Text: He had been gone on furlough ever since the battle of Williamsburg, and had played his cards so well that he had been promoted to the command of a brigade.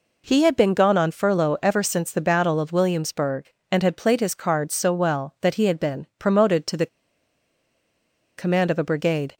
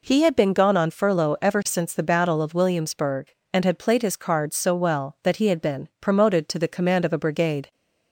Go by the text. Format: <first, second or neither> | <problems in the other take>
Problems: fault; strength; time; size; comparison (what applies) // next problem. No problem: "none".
second | pauses between "the" and "command"; strong; at 6.8 s; 1.5 s long